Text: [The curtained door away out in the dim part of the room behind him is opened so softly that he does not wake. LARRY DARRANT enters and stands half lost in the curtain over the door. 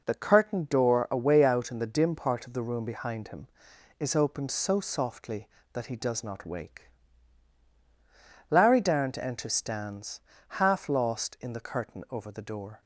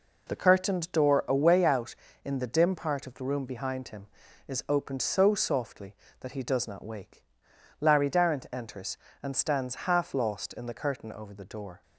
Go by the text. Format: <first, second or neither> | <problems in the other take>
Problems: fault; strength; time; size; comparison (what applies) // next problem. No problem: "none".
second | skips "and"; at 9.5 s // pauses between "stands" and "half"; at 10.1 s; 0.40 s long